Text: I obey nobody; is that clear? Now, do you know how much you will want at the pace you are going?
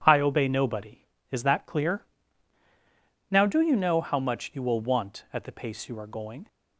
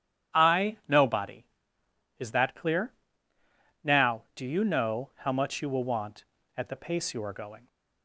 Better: first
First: none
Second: starts louder than the rest; strong; until 1.4 s; 10 dB // skips "obey"; at 0.8 s

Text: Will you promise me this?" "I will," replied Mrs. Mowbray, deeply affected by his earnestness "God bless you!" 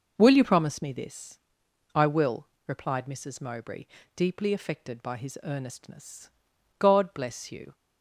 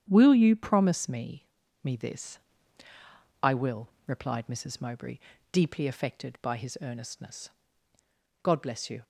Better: first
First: pauses between "earnestness" and "God"; noticeable; at 6.2 s; 0.48 s long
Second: starts louder than the rest; strong; until 1.0 s; 9 dB // says "me" twice; at 1.8 s // pauses between "earnestness" and "God"; noticeable; at 7.4 s; 0.92 s long

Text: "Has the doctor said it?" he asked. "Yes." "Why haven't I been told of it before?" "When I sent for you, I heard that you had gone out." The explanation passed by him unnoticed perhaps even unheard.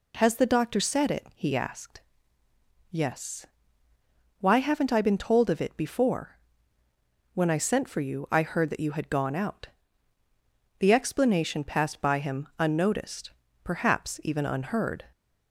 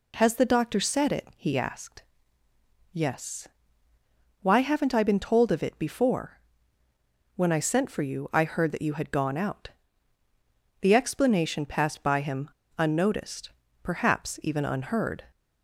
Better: first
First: pauses between "unnoticed" and "perhaps"; slight; at 13.3 s; 0.32 s long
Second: pauses between "him" and "unnoticed"; slight; at 12.4 s; 0.29 s long // pauses between "unnoticed" and "perhaps"; slight; at 13.5 s; 0.32 s long

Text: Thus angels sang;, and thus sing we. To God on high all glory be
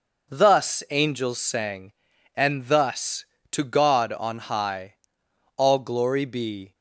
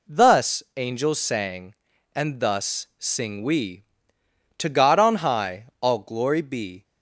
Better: second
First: skips "sing we"; at 3.3 s // pauses between "high" and "all"; noticeable; at 4.9 s; 0.60 s long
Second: none

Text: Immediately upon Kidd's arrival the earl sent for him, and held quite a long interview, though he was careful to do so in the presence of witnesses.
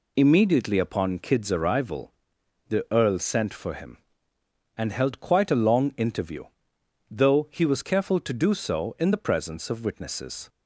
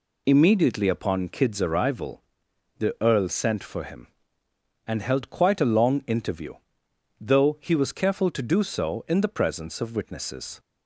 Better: neither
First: pauses between "arrival" and "the"; noticeable; at 2.1 s; 0.56 s long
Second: pauses between "arrival" and "the"; noticeable; at 2.2 s; 0.56 s long

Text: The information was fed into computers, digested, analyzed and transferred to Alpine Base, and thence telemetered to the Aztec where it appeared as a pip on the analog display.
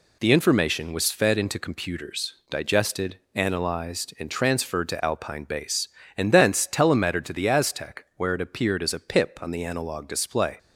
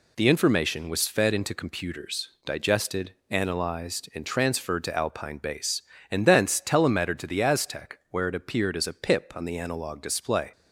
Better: neither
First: none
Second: none

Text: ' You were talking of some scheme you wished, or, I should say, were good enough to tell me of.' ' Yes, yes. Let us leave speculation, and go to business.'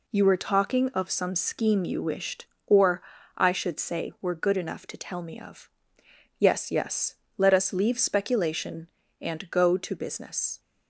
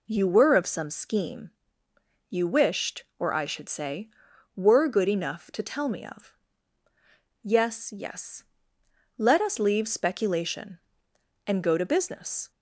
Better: first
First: none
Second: skips "talking"; at 0.5 s // pauses between "scheme" and "you"; noticeable; at 1.5 s; 0.80 s long

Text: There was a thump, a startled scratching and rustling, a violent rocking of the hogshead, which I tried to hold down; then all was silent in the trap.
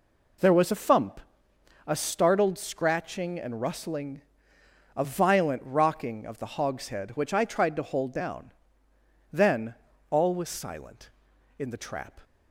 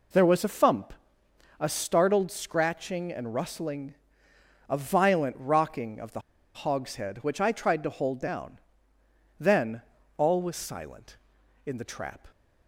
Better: first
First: pauses between "then" and "all"; at 9.7 s; 0.38 s long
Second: pauses between "the" and "hogshead"; at 6.1 s; 0.36 s long // pauses between "then" and "all"; at 9.7 s; 0.38 s long

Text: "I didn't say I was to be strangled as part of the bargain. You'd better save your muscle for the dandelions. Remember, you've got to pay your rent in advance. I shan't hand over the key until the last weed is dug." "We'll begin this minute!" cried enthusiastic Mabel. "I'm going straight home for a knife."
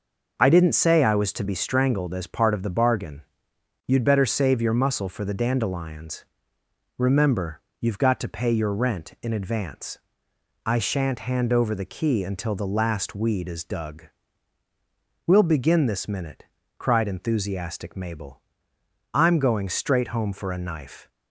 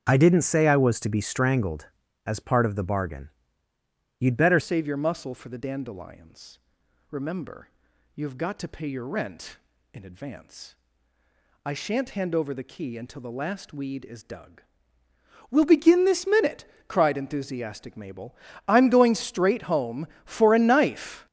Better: first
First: none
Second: starts louder than the rest; strong; until 1.1 s; 7.5 dB // changes voice at "save"; from 4.6 s on; 16.6 s long

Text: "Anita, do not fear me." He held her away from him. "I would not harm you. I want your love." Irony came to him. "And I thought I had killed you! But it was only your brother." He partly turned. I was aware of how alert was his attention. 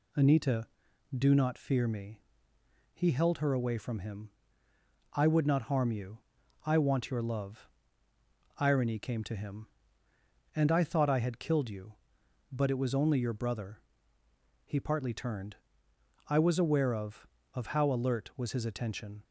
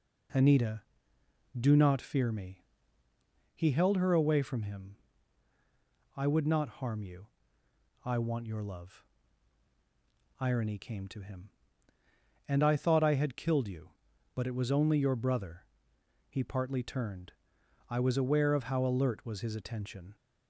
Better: second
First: says "of" twice; at 17.5 s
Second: none

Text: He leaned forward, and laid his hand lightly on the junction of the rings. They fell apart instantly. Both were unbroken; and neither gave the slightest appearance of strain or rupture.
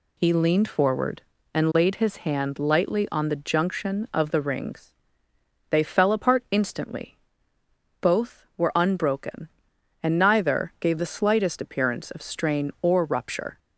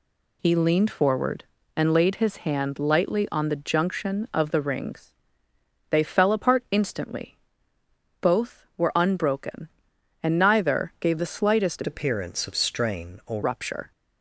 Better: first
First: none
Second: changes voice from "appearance" to "or"; from 11.8 to 13.4 s; 1.6 s long

